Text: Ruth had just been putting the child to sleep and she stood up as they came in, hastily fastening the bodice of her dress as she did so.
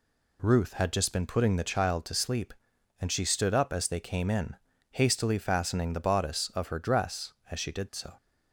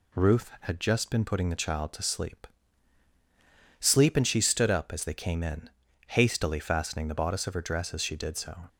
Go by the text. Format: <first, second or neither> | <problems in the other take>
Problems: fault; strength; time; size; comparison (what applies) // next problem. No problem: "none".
first | says "sleep" twice; at 3.8 s